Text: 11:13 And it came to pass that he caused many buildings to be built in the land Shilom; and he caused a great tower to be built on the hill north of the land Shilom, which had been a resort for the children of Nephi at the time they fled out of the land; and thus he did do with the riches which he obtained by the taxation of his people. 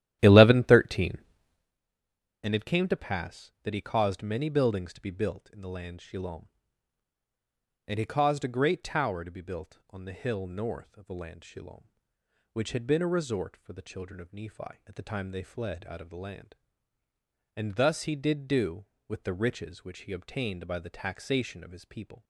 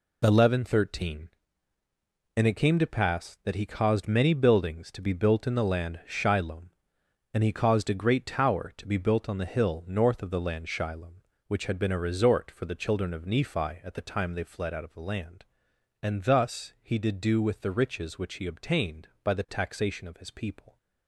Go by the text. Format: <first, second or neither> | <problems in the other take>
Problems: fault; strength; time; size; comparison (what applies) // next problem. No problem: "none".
second | starts louder than the rest; strong; until 1.8 s; 12.5 dB